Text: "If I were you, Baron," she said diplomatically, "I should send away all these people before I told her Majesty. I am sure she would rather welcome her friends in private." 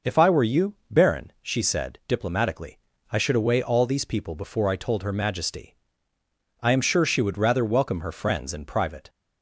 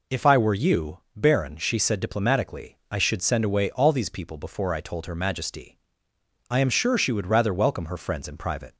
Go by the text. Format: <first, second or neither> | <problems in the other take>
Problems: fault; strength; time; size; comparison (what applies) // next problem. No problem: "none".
second | skips "send"; at 3.3 s